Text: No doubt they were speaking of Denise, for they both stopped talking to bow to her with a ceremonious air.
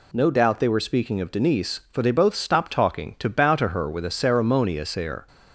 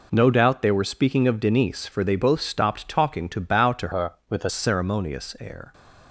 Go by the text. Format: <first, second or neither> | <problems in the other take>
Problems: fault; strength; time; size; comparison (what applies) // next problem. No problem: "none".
first | changes voice from "her" to "a"; from 3.9 to 4.4 s; 0.5 s long